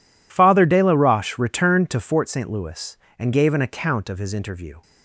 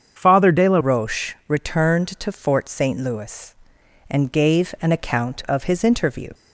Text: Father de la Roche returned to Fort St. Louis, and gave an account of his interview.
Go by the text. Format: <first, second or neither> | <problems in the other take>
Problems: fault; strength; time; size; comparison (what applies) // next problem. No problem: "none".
first | starts louder than the rest; until 1.1 s; 7 dB // changes voice at "Roche"; from 0.8 s on; 5.4 s long